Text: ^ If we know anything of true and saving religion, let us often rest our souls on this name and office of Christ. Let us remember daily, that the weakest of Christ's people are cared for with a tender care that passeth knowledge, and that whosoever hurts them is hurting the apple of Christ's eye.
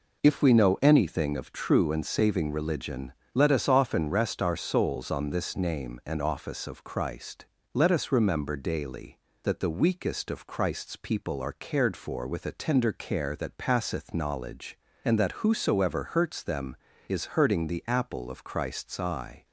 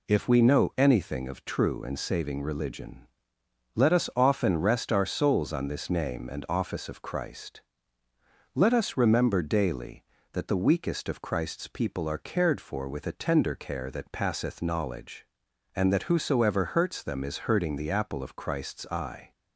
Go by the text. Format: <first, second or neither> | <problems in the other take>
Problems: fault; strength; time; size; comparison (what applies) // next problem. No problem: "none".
neither | none